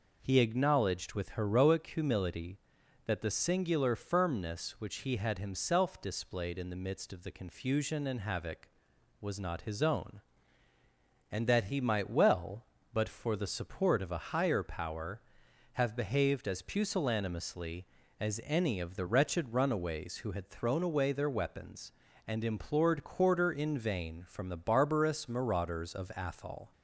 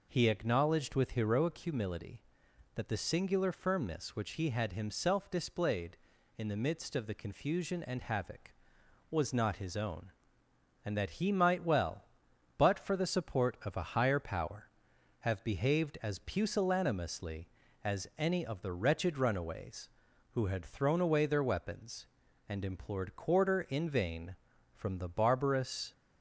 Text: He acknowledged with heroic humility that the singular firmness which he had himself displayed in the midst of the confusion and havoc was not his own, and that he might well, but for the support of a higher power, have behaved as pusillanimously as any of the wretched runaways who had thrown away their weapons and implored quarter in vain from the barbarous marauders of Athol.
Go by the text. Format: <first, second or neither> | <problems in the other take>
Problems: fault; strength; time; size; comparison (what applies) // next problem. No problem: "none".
first | stops before "marauders of Athol"; at 25.9 s